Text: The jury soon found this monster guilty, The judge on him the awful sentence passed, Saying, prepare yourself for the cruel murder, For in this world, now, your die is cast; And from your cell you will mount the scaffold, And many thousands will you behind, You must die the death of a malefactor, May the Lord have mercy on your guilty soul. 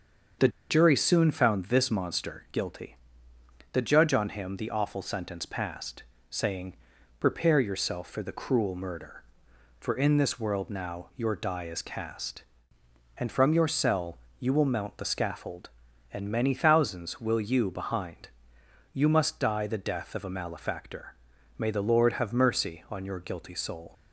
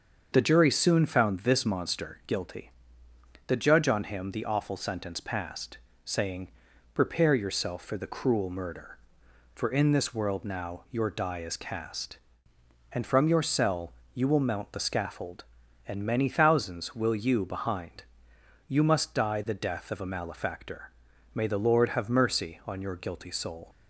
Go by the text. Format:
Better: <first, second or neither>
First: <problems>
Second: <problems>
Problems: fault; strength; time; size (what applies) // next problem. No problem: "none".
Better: second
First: starts louder than the rest; until 1.6 s; 7 dB // pauses between "The" and "jury"; slight; at 0.4 s; 0.21 s long // pauses between "cell" and "you"; slight; at 14.1 s; 0.22 s long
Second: starts louder than the rest; until 1.3 s; 7 dB // pauses between "cell" and "you"; slight; at 13.9 s; 0.22 s long